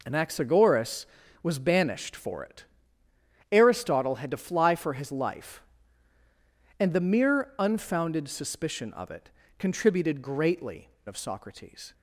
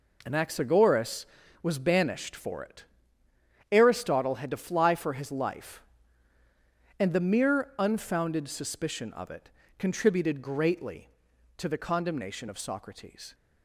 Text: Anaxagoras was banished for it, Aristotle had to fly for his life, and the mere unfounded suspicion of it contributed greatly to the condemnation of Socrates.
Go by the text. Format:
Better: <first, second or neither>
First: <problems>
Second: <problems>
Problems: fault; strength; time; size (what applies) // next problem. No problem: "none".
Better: second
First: pauses between "it" and "contributed"; slight; at 9.2 s; 0.28 s long // skips "to the condemnation"; at 10.9 s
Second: pauses between "it" and "contributed"; slight; at 9.4 s; 0.28 s long